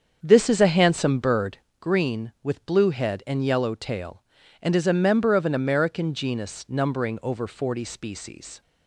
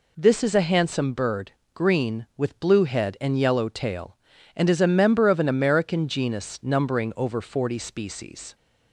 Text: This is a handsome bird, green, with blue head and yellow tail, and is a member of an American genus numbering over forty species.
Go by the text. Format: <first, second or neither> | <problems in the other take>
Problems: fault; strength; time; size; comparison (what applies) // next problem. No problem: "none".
second | starts louder than the rest; strong; until 1.7 s; 7 dB